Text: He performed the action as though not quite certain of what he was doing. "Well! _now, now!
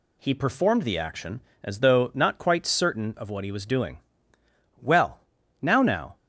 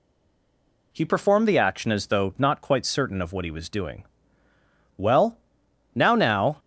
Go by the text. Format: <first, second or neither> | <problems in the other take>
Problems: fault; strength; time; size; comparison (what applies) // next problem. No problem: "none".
first | stays silent before the first word; slight; until 0.9 s; 0.9 s long